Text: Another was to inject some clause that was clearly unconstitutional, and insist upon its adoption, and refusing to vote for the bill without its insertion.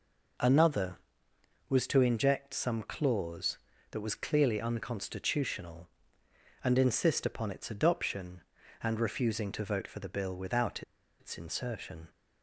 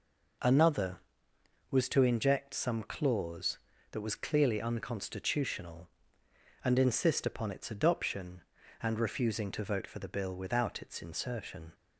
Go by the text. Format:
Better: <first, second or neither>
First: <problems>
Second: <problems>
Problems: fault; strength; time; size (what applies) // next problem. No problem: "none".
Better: second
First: pauses between "without" and "its"; at 10.8 s; 0.38 s long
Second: none